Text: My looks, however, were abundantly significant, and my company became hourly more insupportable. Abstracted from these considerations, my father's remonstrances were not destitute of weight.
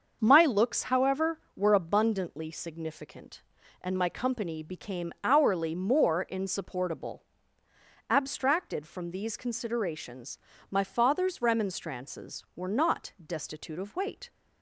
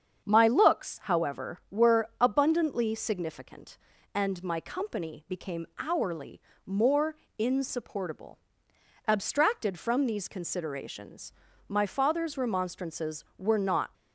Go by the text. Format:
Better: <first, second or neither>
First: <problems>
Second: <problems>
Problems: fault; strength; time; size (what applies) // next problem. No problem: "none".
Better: first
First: starts louder than the rest; until 1.2 s; 6.5 dB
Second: starts louder than the rest; strong; until 1.2 s; 7.5 dB // pauses between "hourly" and "more"; slight; at 6.3 s; 0.26 s long // pauses between "more" and "insupportable"; slight; at 7.1 s; 0.22 s long // stops before "destitute of weight"; at 13.9 s